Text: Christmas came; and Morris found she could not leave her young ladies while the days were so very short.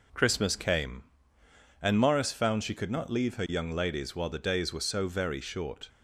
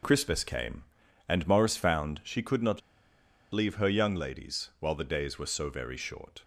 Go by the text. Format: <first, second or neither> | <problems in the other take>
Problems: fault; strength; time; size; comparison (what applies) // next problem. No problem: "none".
first | pauses between "not" and "leave"; noticeable; at 2.8 s; 0.73 s long